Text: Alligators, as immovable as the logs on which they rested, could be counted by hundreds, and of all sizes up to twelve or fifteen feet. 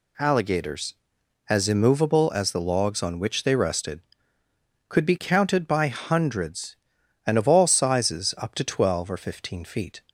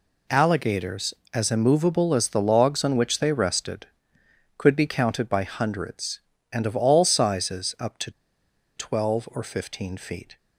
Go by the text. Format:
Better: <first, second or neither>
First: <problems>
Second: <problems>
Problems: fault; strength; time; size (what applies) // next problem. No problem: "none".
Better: first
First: none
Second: pauses between "to" and "twelve"; noticeable; at 8.1 s; 0.64 s long